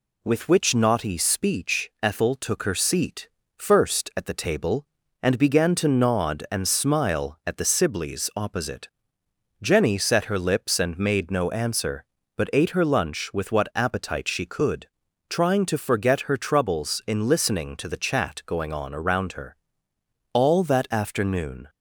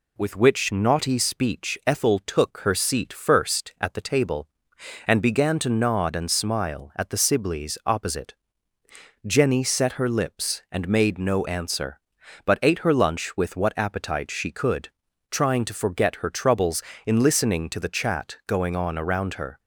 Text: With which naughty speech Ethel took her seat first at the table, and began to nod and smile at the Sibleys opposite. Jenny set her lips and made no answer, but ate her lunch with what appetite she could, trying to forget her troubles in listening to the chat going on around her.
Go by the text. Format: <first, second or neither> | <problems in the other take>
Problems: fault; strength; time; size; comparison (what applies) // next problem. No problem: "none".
second | pauses between "seat" and "first"; slight; at 3.2 s; 0.30 s long // goes on to say "All that afternoon"; from 20.3 s on; 1.3 s long